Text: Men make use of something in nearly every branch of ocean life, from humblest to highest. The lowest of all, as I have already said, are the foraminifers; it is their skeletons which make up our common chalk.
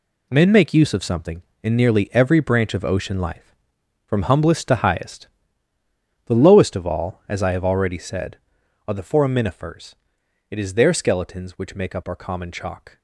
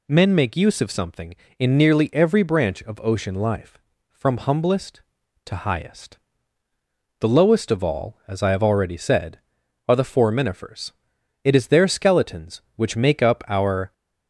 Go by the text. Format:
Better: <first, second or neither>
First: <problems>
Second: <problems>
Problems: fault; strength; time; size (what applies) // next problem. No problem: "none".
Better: first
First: none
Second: stops before "common chalk"; at 13.9 s